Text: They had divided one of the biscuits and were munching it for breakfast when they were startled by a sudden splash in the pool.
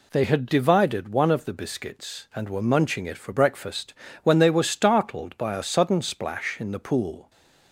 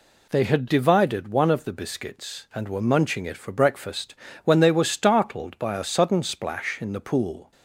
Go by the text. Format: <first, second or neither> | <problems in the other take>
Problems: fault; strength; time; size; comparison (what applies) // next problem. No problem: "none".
neither | pauses between "breakfast" and "when"; slight; the same in both